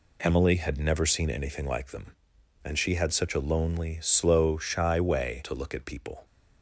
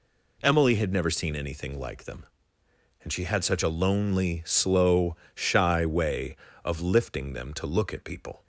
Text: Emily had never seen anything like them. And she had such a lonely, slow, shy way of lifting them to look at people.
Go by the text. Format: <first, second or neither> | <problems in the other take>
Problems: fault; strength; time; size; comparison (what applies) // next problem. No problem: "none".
second | skips "of lifting them"; at 5.4 s